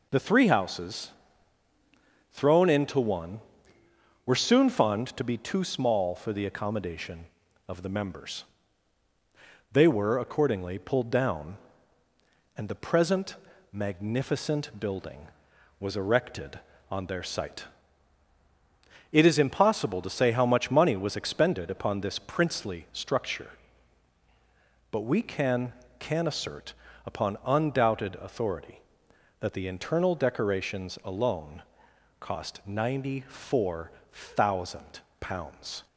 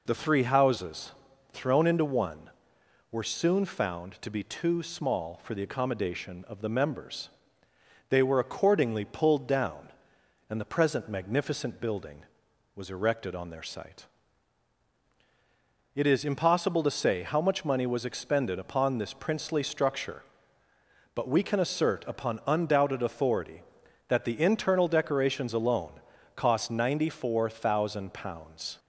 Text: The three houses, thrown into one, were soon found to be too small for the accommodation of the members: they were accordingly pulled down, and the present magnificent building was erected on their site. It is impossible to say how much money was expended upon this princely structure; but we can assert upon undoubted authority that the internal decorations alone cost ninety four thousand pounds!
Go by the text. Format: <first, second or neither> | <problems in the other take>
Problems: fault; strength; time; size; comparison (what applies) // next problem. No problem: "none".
second | pauses between "present" and "magnificent"; at 13.3 s; 0.38 s long // says "can" twice; at 25.9 s // pauses between "assert" and "upon"; slight; at 26.7 s; 0.30 s long // pauses between "alone" and "cost"; noticeable; at 31.6 s; 0.60 s long; also in the second // pauses between "four" and "thousand"; slight; at 33.9 s; 0.20 s long // pauses between "thousand" and "pounds"; slight; at 35.0 s; 0.20 s long